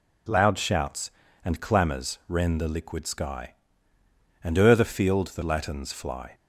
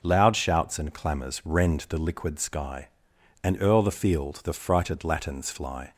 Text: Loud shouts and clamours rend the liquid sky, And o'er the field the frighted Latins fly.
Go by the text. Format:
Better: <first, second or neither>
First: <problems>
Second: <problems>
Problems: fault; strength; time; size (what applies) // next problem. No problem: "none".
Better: second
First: skips "frighted"; at 5.4 s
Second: none